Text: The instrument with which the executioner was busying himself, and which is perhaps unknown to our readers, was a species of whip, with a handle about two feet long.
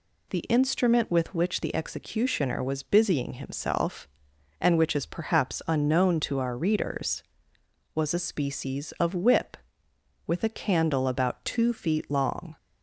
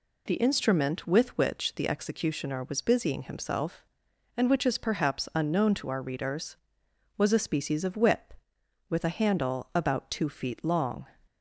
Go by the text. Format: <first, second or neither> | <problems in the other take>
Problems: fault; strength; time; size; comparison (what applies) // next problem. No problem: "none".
second | says "candle" for "handle"; at 10.4 s